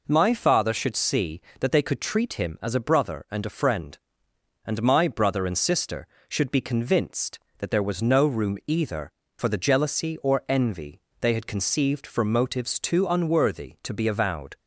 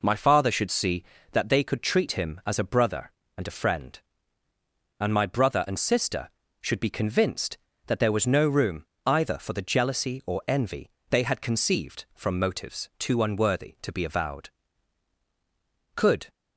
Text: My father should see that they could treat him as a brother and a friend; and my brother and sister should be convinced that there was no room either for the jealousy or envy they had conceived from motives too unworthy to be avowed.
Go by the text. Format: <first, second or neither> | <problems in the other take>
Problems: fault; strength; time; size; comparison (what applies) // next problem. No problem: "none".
first | pauses between "room" and "either"; slight; at 8.8 s; 0.18 s long // pauses between "envy" and "they"; slight; at 10.8 s; 0.22 s long; slight in the first // goes on to say "Could"; slight; from 15.9 s on; 0.32 s long